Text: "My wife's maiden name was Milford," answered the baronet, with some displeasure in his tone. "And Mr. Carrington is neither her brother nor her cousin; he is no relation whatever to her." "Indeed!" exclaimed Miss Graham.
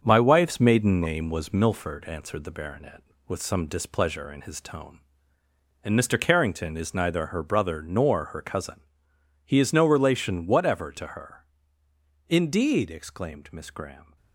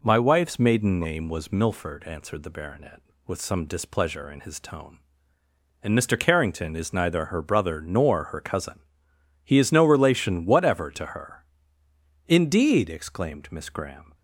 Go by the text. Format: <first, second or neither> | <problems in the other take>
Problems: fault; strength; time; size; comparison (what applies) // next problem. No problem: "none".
second | gets quieter; throughout; 6.5 dB